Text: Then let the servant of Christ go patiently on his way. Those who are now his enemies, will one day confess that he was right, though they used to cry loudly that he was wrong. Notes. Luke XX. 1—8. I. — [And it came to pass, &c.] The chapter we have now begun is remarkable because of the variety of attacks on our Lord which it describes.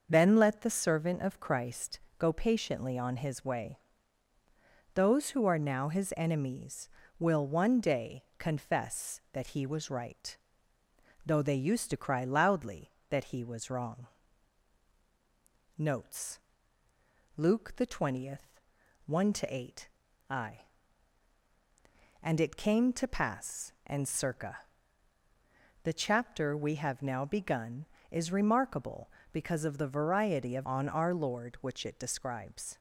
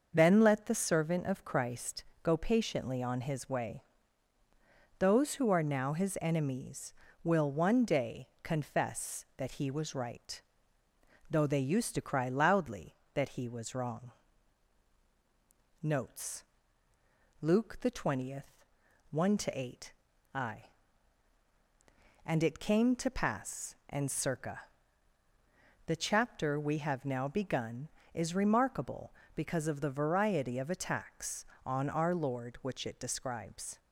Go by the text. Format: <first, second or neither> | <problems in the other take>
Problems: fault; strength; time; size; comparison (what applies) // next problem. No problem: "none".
second | starts louder than the rest; until 1.1 s; 6.5 dB; also in the second // pauses between "Christ" and "go"; slight; at 1.9 s; 0.18 s long; slight in the second // skips "attacks"; at 30.6 s